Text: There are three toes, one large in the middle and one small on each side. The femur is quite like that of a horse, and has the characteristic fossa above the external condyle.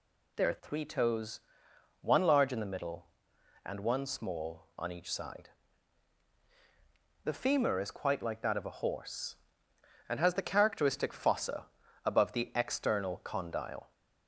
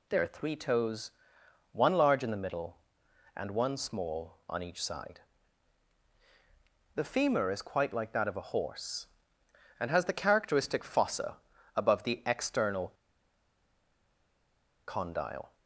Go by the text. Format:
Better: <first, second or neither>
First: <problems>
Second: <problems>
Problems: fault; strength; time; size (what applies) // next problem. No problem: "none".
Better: first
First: pauses between "fossa" and "above"; slight; at 11.6 s; 0.36 s long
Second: pauses between "fossa" and "above"; slight; at 11.3 s; 0.36 s long // pauses between "external" and "condyle"; strong; at 12.8 s; 1.9 s long